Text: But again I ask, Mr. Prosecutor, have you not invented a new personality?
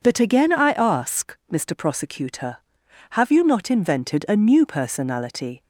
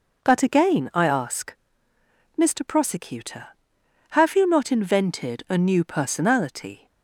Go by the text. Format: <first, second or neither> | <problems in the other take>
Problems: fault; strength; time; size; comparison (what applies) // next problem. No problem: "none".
neither | none